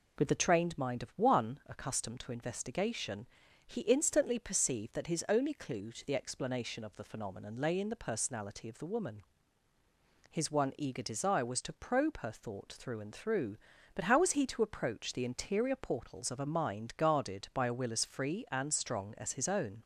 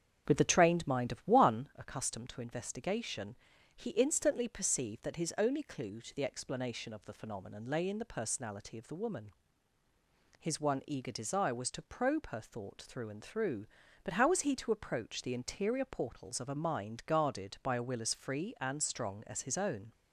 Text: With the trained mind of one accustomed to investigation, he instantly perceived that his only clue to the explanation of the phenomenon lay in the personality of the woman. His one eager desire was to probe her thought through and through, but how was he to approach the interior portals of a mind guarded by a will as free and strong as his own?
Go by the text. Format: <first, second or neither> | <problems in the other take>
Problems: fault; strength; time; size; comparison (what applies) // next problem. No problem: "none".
first | starts louder than the rest; strong; until 1.8 s; 8 dB